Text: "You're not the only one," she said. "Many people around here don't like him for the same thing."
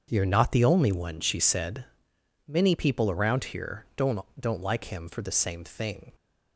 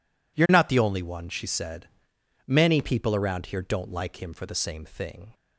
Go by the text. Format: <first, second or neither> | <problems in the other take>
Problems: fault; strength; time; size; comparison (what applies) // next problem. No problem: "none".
second | starts louder than the rest; until 1.1 s; 7 dB // says "don't" twice; at 4.3 s